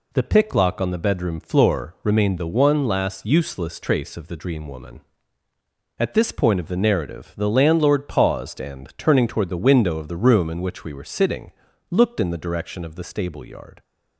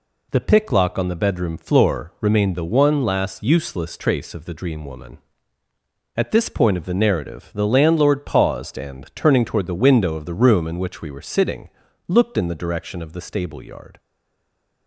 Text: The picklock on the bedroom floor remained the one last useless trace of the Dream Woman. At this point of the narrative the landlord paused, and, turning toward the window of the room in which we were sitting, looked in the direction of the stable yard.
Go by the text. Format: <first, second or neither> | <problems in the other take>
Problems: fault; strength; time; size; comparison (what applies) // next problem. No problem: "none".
first | stays silent after the last word; slight; from 13.9 s on; 0.9 s long